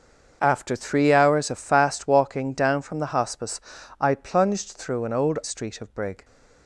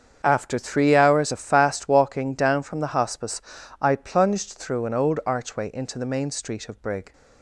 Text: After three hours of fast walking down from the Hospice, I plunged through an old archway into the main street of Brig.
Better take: second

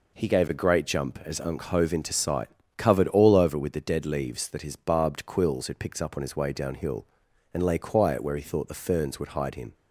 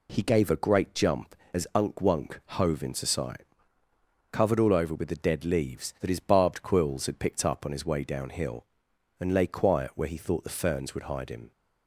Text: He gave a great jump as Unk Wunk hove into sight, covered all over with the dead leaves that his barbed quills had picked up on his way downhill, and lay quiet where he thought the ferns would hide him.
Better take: second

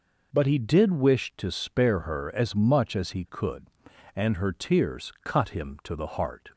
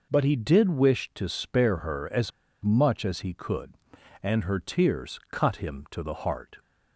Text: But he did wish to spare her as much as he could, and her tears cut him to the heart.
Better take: first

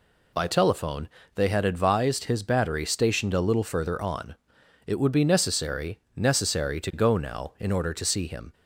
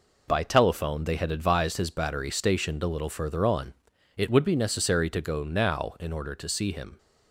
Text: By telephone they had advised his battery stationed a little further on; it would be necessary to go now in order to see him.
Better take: second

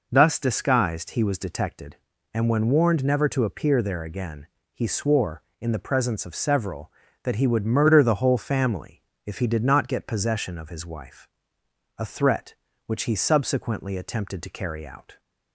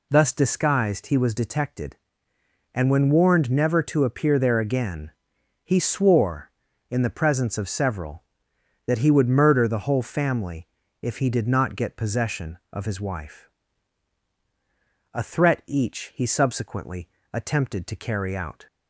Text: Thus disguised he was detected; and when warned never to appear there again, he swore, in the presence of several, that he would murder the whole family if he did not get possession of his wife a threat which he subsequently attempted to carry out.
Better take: first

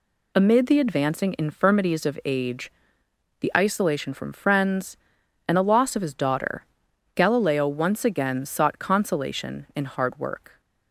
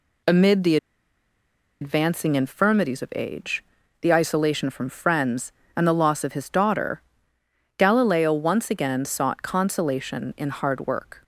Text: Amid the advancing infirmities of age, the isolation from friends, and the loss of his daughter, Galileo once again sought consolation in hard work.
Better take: first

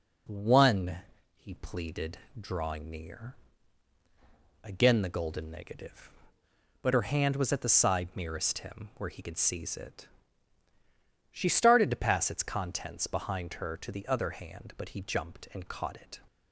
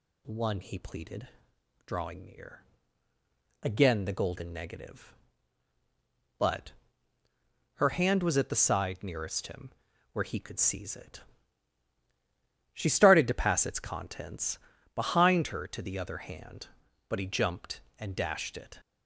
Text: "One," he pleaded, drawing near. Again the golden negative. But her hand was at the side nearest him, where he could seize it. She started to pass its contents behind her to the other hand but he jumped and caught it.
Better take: first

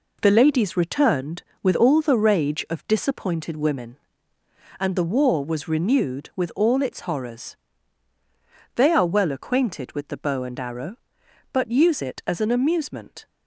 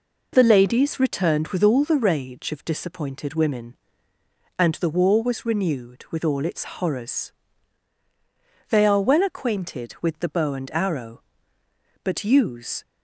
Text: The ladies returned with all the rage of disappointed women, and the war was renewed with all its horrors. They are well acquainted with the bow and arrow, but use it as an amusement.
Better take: first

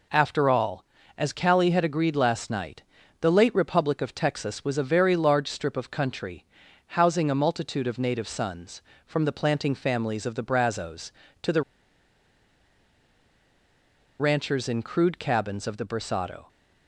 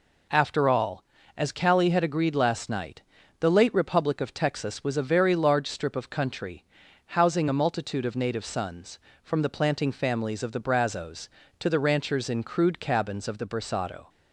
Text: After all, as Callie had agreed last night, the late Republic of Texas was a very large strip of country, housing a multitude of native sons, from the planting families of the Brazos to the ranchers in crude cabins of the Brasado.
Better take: second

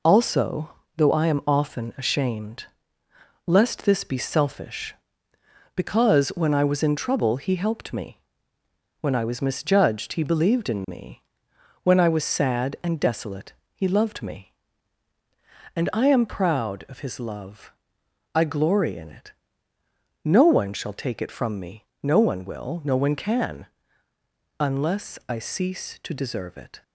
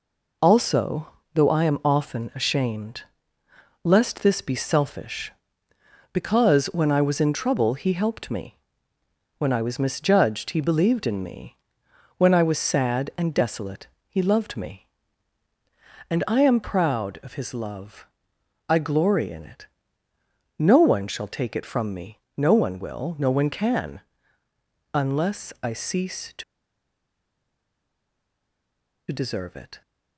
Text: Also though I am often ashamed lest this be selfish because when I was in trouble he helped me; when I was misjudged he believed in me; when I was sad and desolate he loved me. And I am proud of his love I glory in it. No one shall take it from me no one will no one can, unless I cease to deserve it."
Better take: first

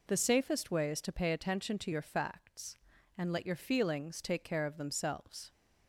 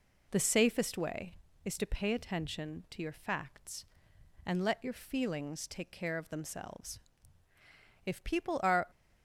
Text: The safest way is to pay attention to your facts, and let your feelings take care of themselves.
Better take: first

